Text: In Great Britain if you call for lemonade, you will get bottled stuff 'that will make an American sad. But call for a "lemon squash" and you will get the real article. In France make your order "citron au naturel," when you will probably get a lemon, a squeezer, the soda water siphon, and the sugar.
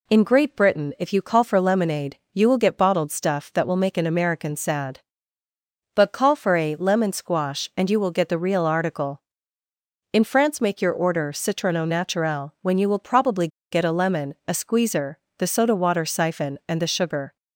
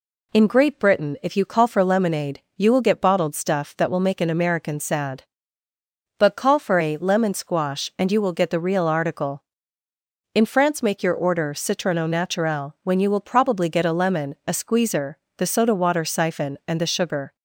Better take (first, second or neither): second